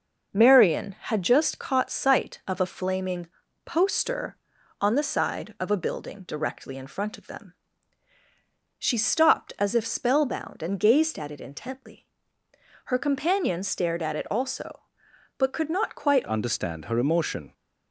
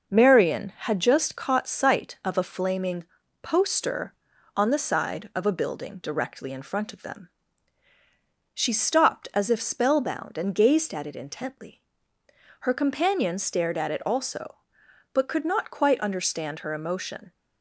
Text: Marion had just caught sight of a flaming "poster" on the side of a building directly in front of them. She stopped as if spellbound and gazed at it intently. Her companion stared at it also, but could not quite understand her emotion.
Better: second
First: starts louder than the rest; noticeable; until 1.4 s; 6 dB // pauses between "flaming" and "poster"; at 3.2 s; 0.38 s long // changes voice at "understand"; from 16.2 s on; 1.3 s long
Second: starts louder than the rest; noticeable; until 1.1 s; 6 dB // pauses between "flaming" and "poster"; at 3.0 s; 0.38 s long

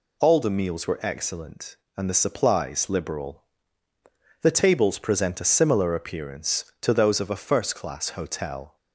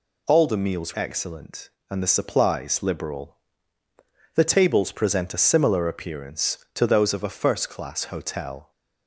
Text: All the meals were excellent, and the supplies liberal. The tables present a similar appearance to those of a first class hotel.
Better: first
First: none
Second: skips "were"; at 0.9 s

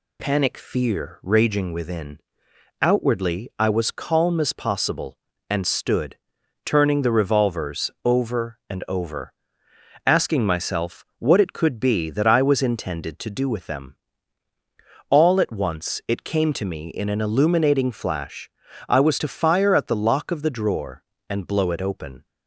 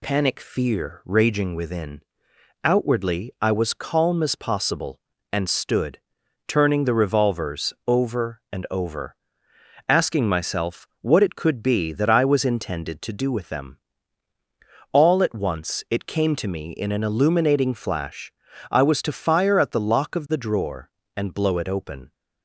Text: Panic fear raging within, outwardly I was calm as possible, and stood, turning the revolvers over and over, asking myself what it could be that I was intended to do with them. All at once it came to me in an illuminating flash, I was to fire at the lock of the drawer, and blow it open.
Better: neither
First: pauses between "revolvers" and "over"; slight; at 7.8 s; 0.16 s long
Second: pauses between "revolvers" and "over"; slight; at 7.7 s; 0.16 s long

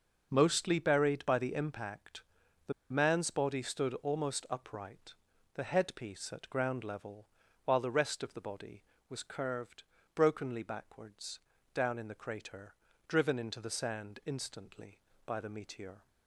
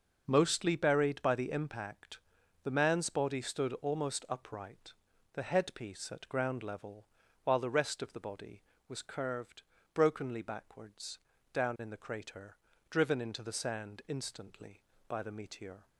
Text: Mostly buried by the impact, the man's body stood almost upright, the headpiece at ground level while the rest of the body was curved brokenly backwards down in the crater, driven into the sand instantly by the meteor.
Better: second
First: pauses between "the" and "man's"; slight; at 2.7 s; 0.20 s long // pauses between "level" and "while"; at 7.2 s; 0.38 s long // pauses between "curved" and "brokenly"; slight; at 9.8 s; 0.32 s long // pauses between "backwards" and "down"; slight; at 11.4 s; 0.34 s long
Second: pauses between "level" and "while"; at 7.0 s; 0.38 s long // pauses between "curved" and "brokenly"; slight; at 9.6 s; 0.32 s long // pauses between "backwards" and "down"; slight; at 11.1 s; 0.34 s long

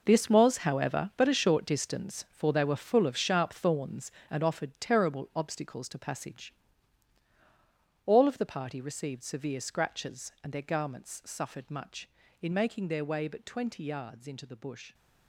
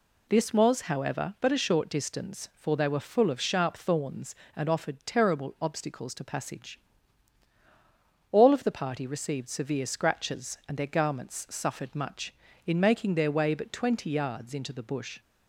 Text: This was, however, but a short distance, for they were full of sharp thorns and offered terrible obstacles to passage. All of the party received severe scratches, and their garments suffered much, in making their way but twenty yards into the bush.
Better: second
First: gets quieter; strong; throughout; 12 dB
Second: none

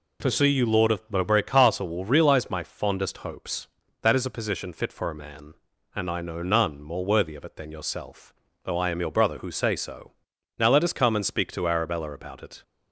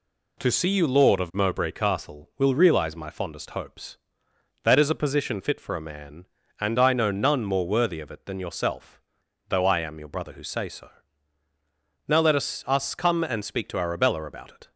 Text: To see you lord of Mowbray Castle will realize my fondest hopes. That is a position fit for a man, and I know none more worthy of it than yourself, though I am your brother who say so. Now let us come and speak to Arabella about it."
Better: first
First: none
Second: says "us" twice; at 12.6 s

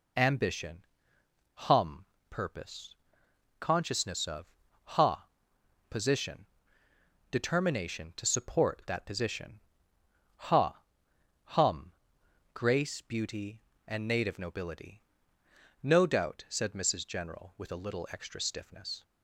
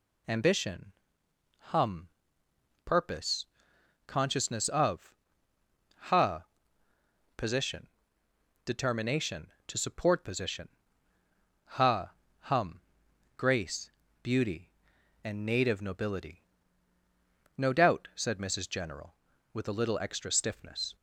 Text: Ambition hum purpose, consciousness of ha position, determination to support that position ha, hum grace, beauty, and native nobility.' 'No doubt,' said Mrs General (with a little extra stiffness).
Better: first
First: pauses between "Ambition" and "hum"; noticeable; at 0.8 s; 0.68 s long // pauses between "hum" and "purpose"; slight; at 2.0 s; 0.26 s long // pauses between "of" and "ha"; slight; at 4.5 s; 0.32 s long // pauses between "ha" and "position"; noticeable; at 5.2 s; 0.60 s long // pauses between "position" and "ha"; noticeable; at 9.6 s; 0.76 s long // pauses between "hum" and "grace"; noticeable; at 11.9 s; 0.62 s long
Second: pauses between "Ambition" and "hum"; noticeable; at 0.9 s; 0.66 s long // pauses between "hum" and "purpose"; noticeable; at 2.0 s; 0.78 s long // pauses between "of" and "ha"; noticeable; at 5.1 s; 0.86 s long // pauses between "ha" and "position"; noticeable; at 6.4 s; 0.92 s long // skips "that"; at 10.2 s // pauses between "position" and "ha"; noticeable; at 10.6 s; 0.96 s long // pauses between "hum" and "grace"; noticeable; at 12.7 s; 0.58 s long

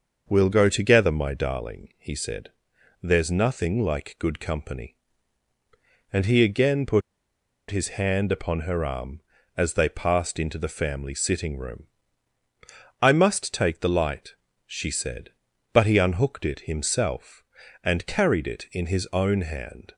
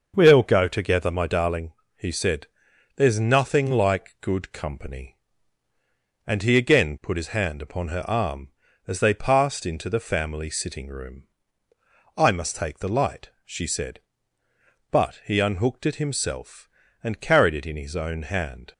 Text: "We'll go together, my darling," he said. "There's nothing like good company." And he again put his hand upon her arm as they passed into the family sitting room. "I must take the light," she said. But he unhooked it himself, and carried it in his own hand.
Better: second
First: starts louder than the rest; until 1.2 s; 6 dB // pauses between "put" and "his"; noticeable; at 7.0 s; 0.69 s long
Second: starts louder than the rest; noticeable; until 1.1 s; 6 dB

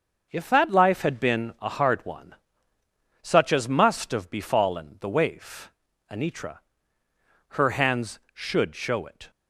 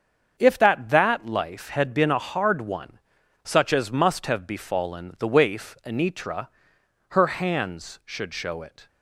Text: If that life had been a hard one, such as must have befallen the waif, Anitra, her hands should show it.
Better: first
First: starts louder than the rest; until 1.3 s; 6.5 dB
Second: starts louder than the rest; strong; until 1.4 s; 7 dB // says "that" twice; at 0.8 s

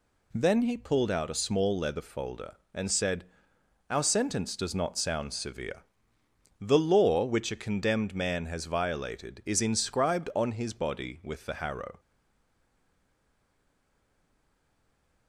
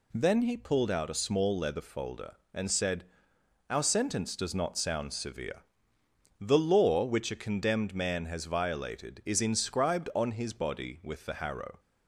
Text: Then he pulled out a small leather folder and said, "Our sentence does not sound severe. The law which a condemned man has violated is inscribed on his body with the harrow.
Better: second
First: stays silent after the last word; strong; from 11.9 s on; 3.3 s long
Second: none

